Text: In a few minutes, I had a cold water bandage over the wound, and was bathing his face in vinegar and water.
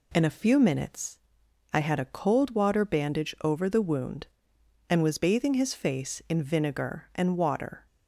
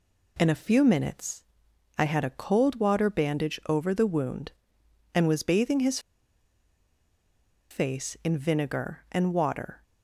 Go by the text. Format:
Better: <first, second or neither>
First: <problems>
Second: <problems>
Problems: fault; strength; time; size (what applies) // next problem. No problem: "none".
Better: first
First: none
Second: pauses between "his" and "face"; strong; at 5.9 s; 1.7 s long